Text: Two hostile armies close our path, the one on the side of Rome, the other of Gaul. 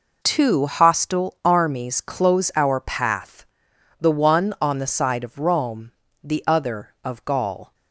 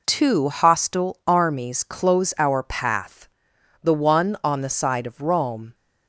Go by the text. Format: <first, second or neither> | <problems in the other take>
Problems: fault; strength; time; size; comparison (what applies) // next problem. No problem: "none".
first | stops before "the other of Gaul"; at 5.7 s